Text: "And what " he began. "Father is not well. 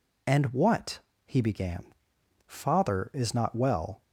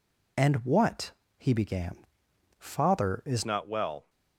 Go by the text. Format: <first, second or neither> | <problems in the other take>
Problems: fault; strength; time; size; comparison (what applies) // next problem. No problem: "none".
first | changes voice at "not"; from 3.4 s on; 0.6 s long